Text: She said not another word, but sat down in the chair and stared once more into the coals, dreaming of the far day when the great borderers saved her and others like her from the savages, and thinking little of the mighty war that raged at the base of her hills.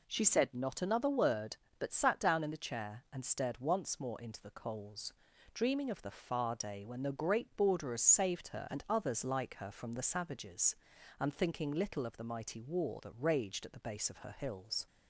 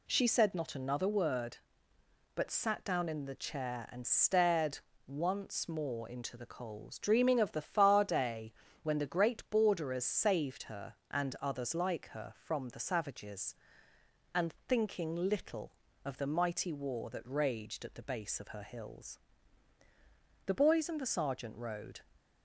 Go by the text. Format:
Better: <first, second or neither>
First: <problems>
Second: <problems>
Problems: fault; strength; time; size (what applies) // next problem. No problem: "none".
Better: first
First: none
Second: pauses between "stared" and "once"; slight; at 4.7 s; 0.26 s long // pauses between "day" and "when"; slight; at 8.5 s; 0.30 s long // goes on to say "The boys and the sergeant rode"; from 20.4 s on; 1.5 s long